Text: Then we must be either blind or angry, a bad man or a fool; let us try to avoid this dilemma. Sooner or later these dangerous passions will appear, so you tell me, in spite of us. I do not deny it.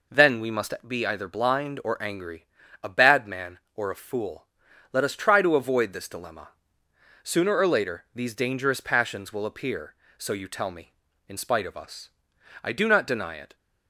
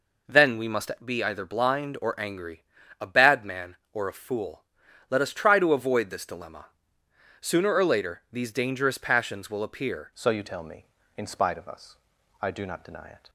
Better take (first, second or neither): first